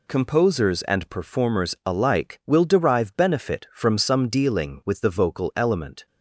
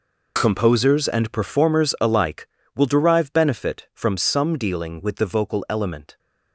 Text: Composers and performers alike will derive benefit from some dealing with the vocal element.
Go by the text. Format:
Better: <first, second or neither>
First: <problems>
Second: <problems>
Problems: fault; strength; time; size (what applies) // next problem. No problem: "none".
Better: neither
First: none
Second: none